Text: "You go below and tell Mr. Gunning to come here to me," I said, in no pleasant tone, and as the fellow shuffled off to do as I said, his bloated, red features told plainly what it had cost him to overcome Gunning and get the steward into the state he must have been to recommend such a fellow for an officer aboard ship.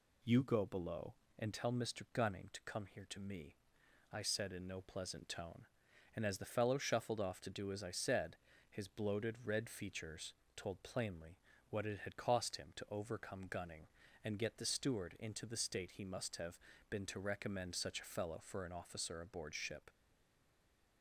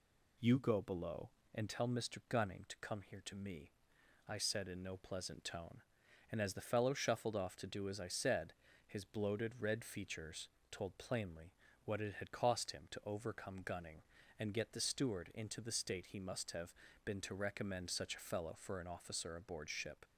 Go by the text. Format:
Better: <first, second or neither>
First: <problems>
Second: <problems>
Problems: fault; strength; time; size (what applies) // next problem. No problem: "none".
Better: second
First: pauses between "features" and "told"; slight; at 10.3 s; 0.20 s long // pauses between "plainly" and "what"; slight; at 11.3 s; 0.32 s long // pauses between "have" and "been"; slight; at 16.5 s; 0.32 s long // stays silent after the last word; from 19.8 s on; 1.2 s long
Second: pauses between "features" and "told"; slight; at 10.4 s; 0.20 s long // pauses between "plainly" and "what"; slight; at 11.5 s; 0.32 s long // pauses between "have" and "been"; slight; at 16.7 s; 0.32 s long